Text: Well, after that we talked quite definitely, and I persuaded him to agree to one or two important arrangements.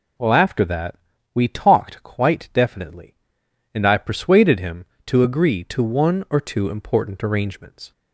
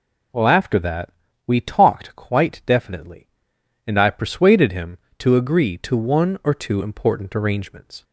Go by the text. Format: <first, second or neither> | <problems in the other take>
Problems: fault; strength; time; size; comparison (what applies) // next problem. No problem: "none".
neither | pauses between "that" and "we"; the same in both